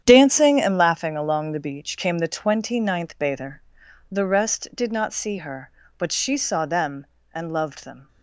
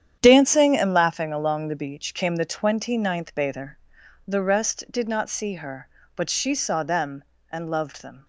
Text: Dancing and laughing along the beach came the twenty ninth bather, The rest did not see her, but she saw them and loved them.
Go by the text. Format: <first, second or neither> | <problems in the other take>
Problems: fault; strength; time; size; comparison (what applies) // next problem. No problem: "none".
neither | starts louder than the rest; strong; the same in both